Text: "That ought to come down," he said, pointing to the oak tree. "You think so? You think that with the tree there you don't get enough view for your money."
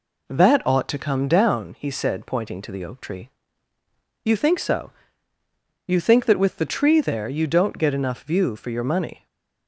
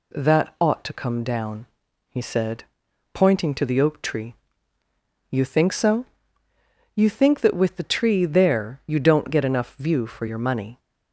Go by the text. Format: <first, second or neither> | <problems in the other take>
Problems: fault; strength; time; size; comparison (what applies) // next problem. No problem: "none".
second | starts louder than the rest; slight; until 1.8 s; 3 dB // stays silent after the last word; slight; from 9.1 s on; 0.5 s long